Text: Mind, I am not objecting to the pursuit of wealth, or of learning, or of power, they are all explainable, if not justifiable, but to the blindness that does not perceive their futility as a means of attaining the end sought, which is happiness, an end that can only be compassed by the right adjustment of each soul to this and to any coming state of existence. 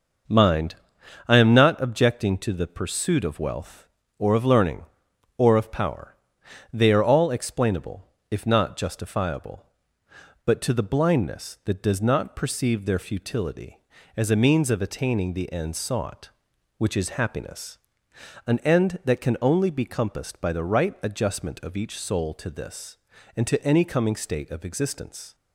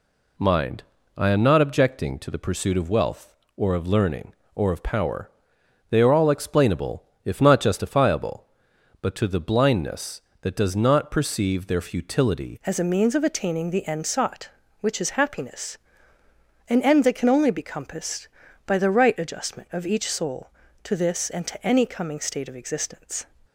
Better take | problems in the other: first | changes voice at "as"; from 12.6 s on; 10.6 s long

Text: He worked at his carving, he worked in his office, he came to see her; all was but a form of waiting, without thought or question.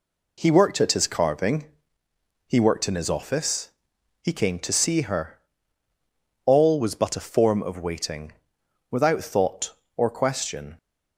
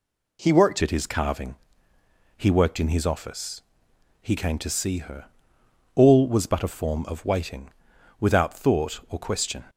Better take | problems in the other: first | changes voice at "at"; from 0.8 s on; 8.8 s long

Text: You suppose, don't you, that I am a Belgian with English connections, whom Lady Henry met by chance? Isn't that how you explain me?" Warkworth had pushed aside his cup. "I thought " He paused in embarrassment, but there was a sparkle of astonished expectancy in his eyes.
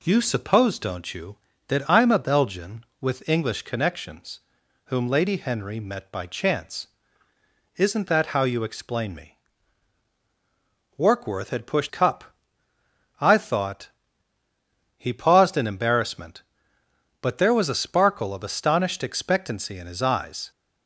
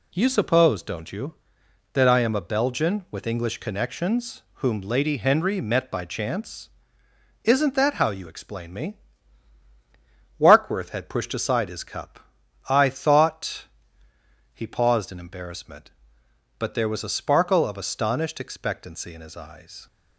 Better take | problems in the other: second | skips "aside his"; at 11.8 s

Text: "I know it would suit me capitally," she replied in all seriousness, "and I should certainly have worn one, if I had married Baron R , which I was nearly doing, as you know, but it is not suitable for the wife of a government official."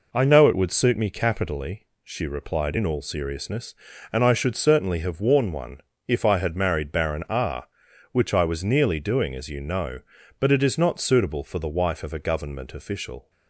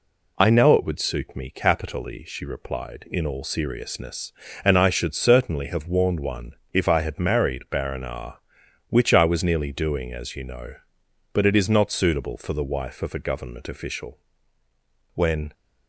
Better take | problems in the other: first | goes on to say "When"; slight; from 15.1 s on; 0.38 s long

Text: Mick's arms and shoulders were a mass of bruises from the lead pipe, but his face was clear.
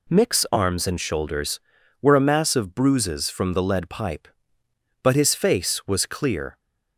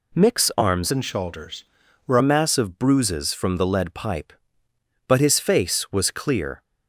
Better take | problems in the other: first | changes voice from "and" to "were"; from 0.8 to 2.1 s; 1.3 s long

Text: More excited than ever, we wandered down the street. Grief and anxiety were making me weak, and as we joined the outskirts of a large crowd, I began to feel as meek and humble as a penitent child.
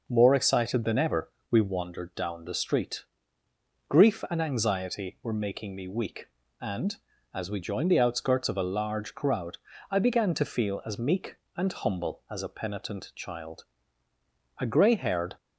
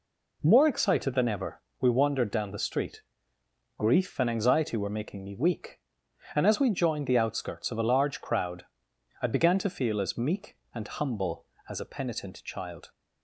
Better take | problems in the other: second | goes on to say "A gray haired"; noticeable; from 14.5 s on; 0.78 s long

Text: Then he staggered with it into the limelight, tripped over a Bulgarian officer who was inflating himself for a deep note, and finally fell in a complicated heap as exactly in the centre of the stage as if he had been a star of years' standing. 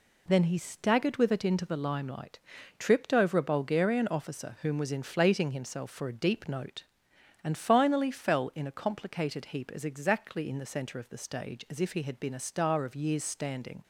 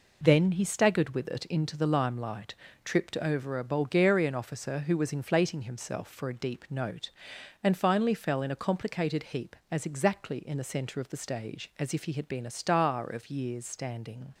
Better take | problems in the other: second | says "whom" for "who"; at 4.6 s

